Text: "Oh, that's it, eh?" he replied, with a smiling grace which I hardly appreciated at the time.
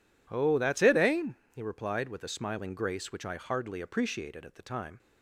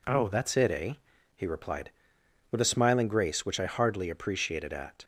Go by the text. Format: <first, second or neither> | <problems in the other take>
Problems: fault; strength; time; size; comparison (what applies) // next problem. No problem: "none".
first | stops before "the time"; at 5.0 s